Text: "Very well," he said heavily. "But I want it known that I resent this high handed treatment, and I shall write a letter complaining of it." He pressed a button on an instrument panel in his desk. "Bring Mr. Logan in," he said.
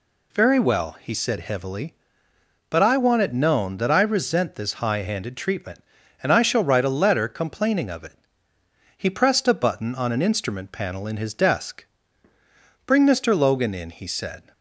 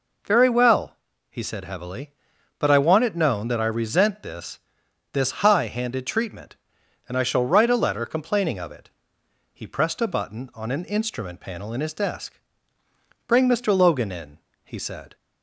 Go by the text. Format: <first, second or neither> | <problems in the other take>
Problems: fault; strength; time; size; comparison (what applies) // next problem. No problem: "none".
first | says "this" twice; at 5.1 s